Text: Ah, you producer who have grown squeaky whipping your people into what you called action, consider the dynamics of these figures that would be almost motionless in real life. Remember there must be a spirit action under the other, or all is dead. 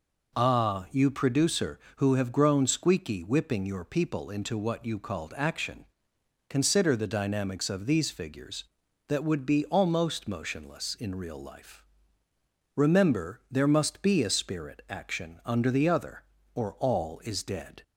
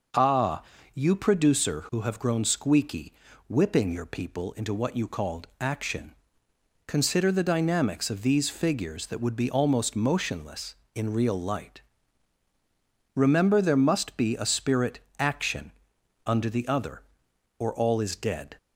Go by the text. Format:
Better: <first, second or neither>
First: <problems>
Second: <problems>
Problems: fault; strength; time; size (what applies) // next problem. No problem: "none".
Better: first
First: none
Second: pauses between "squeaky" and "whipping"; slight; at 3.1 s; 0.36 s long // says "light" for "life"; at 11.3 s // pauses between "spirit" and "action"; slight; at 14.9 s; 0.20 s long // pauses between "action" and "under"; noticeable; at 15.7 s; 0.54 s long